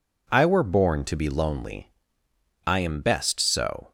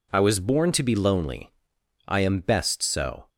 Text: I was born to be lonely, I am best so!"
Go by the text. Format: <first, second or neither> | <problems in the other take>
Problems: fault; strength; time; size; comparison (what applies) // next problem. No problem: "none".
second | says "were" for "was"; at 0.4 s